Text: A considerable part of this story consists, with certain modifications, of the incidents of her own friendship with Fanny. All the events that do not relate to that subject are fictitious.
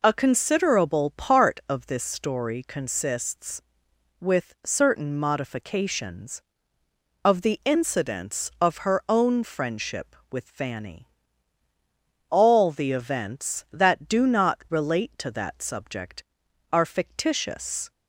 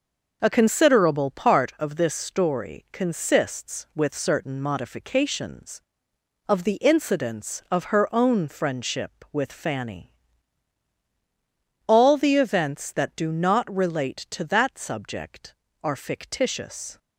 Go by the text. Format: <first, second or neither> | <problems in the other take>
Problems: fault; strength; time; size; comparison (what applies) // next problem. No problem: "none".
neither | none